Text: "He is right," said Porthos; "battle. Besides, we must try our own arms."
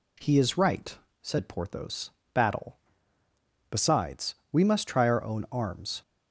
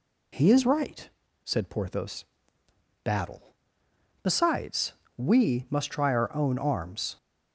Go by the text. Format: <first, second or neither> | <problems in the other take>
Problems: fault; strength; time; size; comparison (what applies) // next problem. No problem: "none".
neither | none